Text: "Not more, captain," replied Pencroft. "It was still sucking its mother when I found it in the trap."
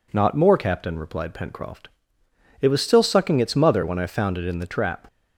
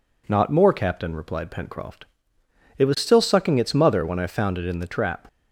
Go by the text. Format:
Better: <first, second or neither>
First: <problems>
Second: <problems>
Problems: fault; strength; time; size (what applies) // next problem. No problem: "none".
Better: neither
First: none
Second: none